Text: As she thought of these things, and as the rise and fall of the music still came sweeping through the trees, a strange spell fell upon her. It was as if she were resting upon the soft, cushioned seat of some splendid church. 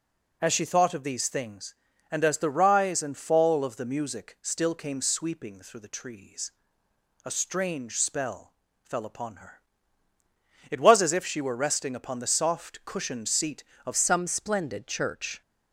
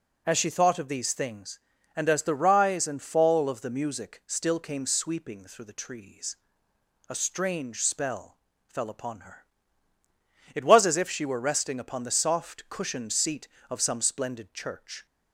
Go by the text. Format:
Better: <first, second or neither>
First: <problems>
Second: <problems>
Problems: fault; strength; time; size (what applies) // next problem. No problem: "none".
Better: second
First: pauses between "spell" and "fell"; slight; at 8.5 s; 0.30 s long // changes voice at "some"; from 13.9 s on; 1.5 s long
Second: pauses between "spell" and "fell"; slight; at 8.3 s; 0.30 s long